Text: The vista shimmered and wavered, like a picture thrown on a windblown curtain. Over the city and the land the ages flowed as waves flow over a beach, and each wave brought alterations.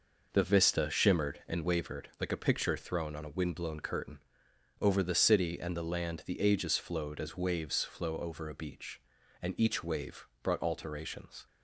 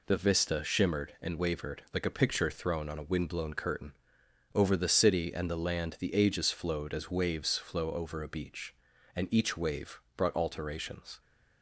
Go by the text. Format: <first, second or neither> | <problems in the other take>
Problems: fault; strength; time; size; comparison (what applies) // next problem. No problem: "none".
second | starts louder than the rest; noticeable; until 2.0 s; 5.5 dB // pauses between "wave" and "brought"; slight; at 10.2 s; 0.16 s long; slight in the second